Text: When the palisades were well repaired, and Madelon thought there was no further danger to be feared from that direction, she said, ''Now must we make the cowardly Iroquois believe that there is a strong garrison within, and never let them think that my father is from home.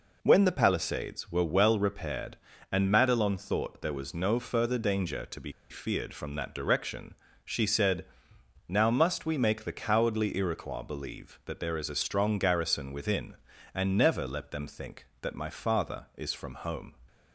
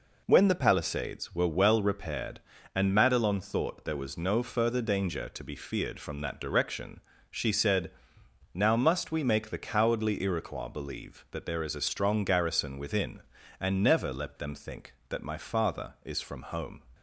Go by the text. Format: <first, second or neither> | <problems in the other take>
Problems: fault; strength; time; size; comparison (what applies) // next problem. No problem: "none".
second | pauses between "be" and "feared"; slight; at 5.5 s; 0.20 s long